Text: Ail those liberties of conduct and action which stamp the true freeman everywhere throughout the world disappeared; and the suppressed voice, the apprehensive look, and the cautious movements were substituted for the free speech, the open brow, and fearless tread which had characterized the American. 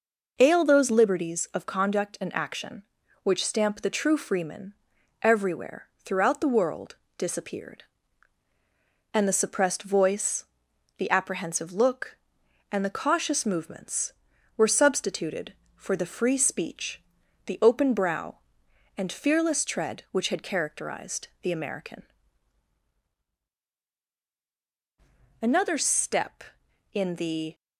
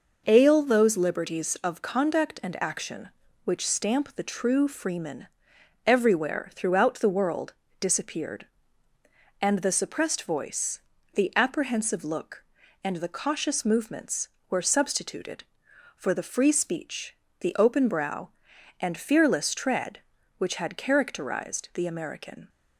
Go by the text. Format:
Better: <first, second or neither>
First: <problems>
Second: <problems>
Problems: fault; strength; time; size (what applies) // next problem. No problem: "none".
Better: second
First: pauses between "freeman" and "everywhere"; noticeable; at 4.7 s; 0.50 s long // pauses between "everywhere" and "throughout"; slight; at 5.8 s; 0.18 s long // pauses between "world" and "disappeared"; slight; at 6.9 s; 0.20 s long // goes on to say "Another step in the"; strong; from 25.5 s on; 2.0 s long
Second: pauses between "freeman" and "everywhere"; noticeable; at 5.2 s; 0.58 s long // pauses between "world" and "disappeared"; slight; at 7.5 s; 0.26 s long